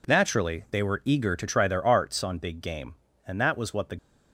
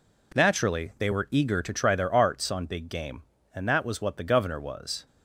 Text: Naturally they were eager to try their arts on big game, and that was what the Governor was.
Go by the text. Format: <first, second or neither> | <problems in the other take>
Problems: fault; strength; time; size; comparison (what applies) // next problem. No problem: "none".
second | stops before "Governor was"; at 3.9 s